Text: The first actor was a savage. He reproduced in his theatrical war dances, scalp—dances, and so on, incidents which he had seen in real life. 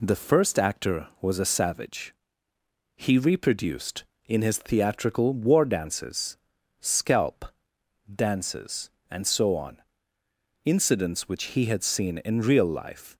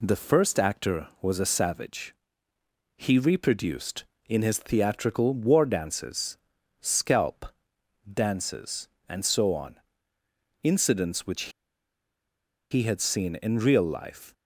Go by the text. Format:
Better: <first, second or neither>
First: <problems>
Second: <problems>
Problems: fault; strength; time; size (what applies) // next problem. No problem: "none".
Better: first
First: none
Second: pauses between "which" and "he"; at 11.5 s; 1.2 s long